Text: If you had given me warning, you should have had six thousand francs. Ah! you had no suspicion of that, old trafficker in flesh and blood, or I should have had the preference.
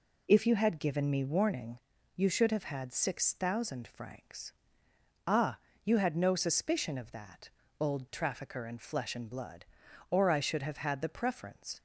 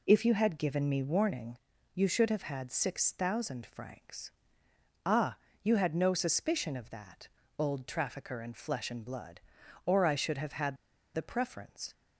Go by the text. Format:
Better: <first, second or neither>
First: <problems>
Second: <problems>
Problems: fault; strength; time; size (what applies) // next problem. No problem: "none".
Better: first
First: none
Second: pauses between "had" and "the"; at 10.7 s; 0.40 s long